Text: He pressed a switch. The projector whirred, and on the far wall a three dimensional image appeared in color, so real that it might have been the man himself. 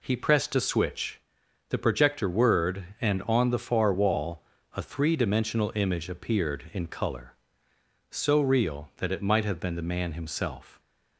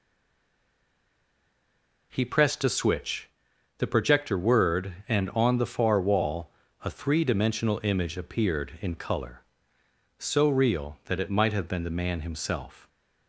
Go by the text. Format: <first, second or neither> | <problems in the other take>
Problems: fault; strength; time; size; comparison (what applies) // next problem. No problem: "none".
first | stays silent before the first word; until 2.1 s; 2.1 s long // pauses between "wall" and "a"; slight; at 6.4 s; 0.34 s long; slight in the first